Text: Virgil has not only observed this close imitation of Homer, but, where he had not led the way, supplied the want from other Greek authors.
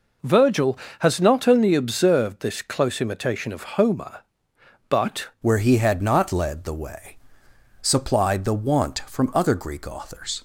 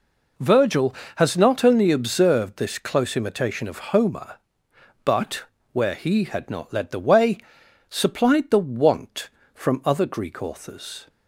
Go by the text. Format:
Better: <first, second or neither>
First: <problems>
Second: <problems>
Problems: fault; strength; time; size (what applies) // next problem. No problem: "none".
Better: second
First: changes voice at "where"; from 5.4 s on; 5.0 s long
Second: none